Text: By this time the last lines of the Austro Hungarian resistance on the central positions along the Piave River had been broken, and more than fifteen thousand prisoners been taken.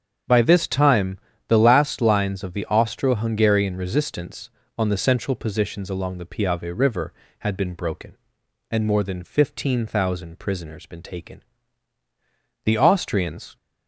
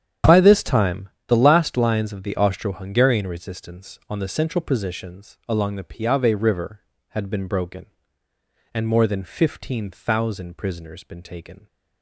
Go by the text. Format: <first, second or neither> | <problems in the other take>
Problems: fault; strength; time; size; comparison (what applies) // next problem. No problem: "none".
second | starts louder than the rest; strong; until 1.5 s; 8 dB; strong in the second // pauses between "time" and "the"; slight; at 1.1 s; 0.30 s long; slight in the second // goes on to say "The Austrians"; noticeable; from 12.6 s on; 0.94 s long